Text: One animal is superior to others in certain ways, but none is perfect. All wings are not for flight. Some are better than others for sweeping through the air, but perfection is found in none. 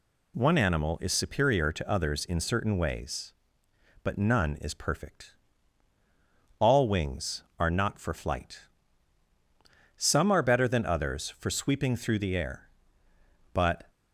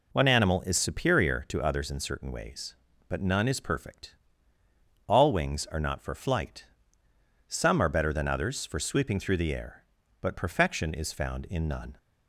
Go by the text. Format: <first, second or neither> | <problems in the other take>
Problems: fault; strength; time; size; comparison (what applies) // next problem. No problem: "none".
second | stops before "perfection is found in none"; at 13.8 s